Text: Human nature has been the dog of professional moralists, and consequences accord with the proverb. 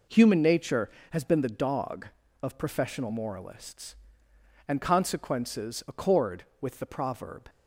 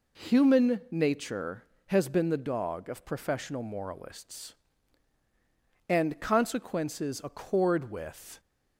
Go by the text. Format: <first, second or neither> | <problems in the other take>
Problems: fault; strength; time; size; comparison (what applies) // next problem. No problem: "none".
first | stops before "the proverb"; at 8.3 s